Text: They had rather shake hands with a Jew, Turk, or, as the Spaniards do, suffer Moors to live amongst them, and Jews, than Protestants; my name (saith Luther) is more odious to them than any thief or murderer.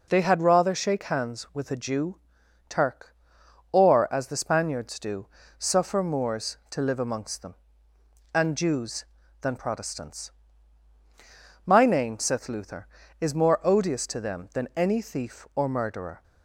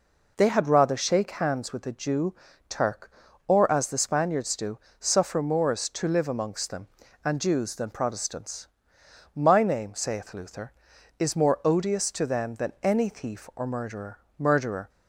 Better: first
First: none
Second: says "murderer" twice; at 14.3 s

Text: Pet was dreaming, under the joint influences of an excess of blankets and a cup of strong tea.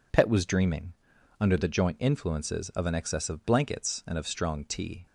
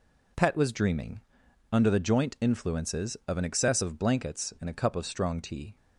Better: second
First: skips "a cup"; at 4.1 s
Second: none

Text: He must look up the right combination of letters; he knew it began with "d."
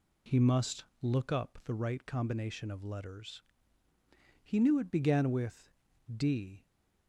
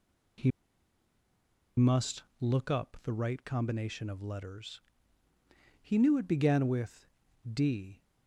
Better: first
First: pauses between "must" and "look"; slight; at 0.8 s; 0.18 s long // pauses between "with" and "d"; at 5.7 s; 0.44 s long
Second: pauses between "He" and "must"; strong; at 0.5 s; 1.2 s long // pauses between "must" and "look"; slight; at 2.2 s; 0.18 s long // pauses between "with" and "d"; at 7.0 s; 0.44 s long

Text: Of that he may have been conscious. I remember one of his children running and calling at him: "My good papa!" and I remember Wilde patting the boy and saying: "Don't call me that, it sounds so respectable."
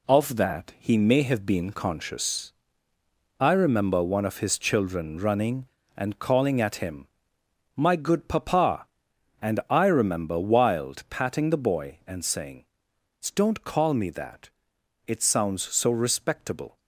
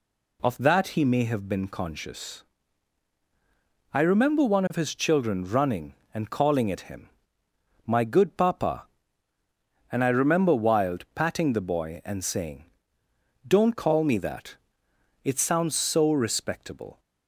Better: second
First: gets quieter; noticeable; throughout; 5.5 dB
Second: none

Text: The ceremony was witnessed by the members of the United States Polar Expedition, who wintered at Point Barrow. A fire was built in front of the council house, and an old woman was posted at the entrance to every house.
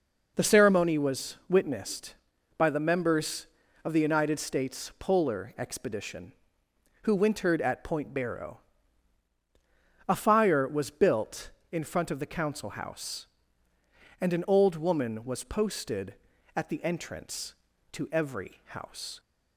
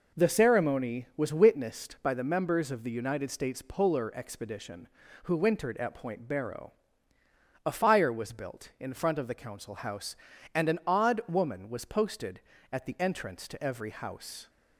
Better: first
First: none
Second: says "odd" for "old"; at 10.8 s

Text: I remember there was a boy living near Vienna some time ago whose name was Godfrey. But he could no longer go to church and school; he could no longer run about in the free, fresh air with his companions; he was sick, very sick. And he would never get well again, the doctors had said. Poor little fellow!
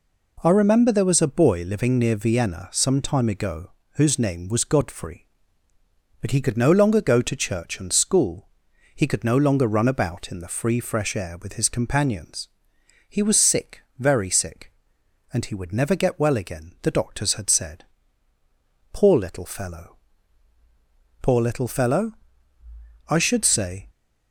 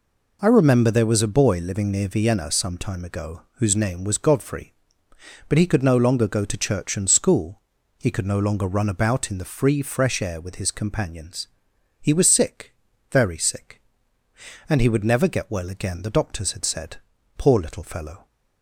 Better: second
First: pauses between "ago" and "whose"; slight; at 3.7 s; 0.26 s long // goes on to say "Poor little fellow I should say"; strong; from 21.2 s on; 2.6 s long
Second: none

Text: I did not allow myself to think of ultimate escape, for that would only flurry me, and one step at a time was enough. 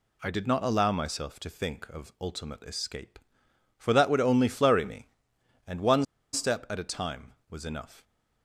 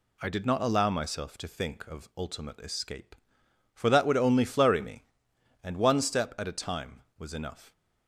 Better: second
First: pauses between "one" and "step"; slight; at 6.0 s; 0.29 s long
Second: none

